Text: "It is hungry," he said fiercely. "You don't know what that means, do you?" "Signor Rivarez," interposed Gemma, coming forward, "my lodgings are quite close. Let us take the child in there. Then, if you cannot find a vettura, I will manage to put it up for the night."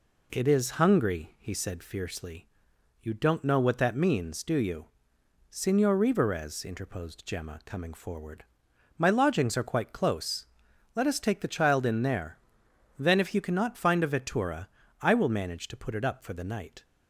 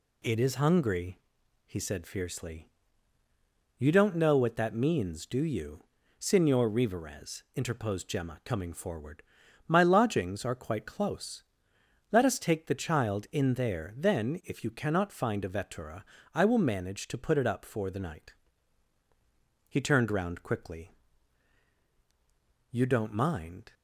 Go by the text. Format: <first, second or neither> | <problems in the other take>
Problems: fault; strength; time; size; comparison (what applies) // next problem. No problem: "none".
first | goes on to say "He turned round quickly You don't mind"; strong; from 19.6 s on; 4.0 s long